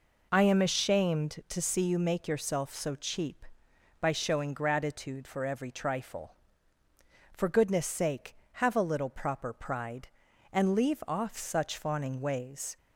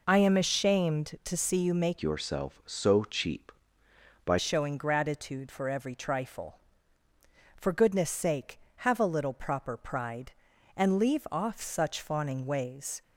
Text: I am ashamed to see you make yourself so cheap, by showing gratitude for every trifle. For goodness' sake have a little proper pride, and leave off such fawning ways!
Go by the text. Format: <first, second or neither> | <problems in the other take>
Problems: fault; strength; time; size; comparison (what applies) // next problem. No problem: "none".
first | changes voice from "yourself" to "by"; from 2.0 to 4.3 s; 2.3 s long